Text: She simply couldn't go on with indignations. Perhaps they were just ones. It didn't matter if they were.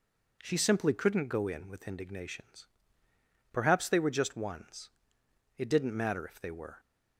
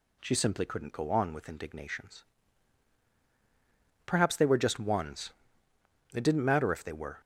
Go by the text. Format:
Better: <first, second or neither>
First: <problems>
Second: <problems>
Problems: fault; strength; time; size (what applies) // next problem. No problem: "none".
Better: second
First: says "in" for "on"; at 1.4 s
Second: none